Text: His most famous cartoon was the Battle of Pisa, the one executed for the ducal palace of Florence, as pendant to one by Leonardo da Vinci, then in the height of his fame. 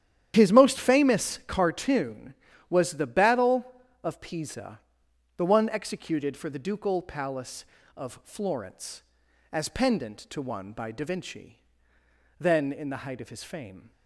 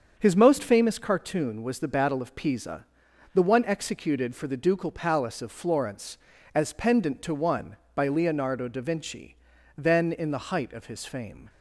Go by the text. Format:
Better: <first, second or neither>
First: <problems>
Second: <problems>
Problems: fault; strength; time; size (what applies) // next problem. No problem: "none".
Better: second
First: starts louder than the rest; strong; until 1.3 s; 10.5 dB // skips "Leonardo"; at 10.9 s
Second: starts louder than the rest; until 1.1 s; 7 dB